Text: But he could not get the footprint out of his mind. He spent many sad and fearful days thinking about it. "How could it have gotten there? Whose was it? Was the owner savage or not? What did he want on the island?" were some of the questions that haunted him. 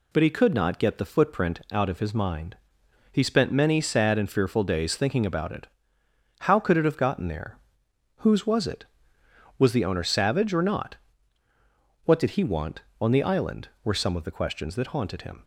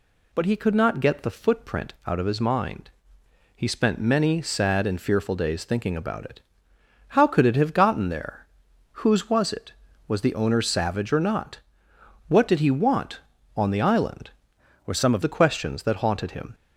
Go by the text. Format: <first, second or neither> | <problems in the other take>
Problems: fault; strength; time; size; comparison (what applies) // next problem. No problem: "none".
first | changes voice from "were" to "of"; from 14.8 to 15.2 s; 0.4 s long